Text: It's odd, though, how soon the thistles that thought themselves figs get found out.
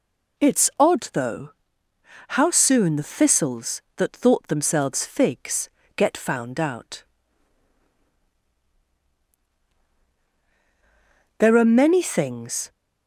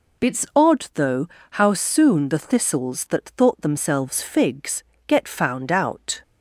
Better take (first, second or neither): second